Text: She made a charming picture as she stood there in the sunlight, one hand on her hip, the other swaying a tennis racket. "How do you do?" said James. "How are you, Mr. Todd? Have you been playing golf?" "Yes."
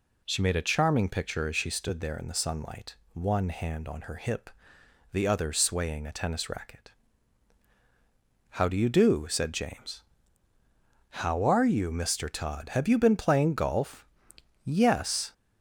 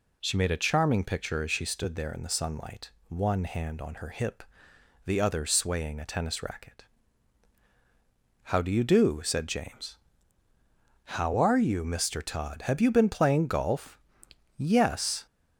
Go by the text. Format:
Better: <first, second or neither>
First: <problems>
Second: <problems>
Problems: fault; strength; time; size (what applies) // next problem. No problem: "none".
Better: neither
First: none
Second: none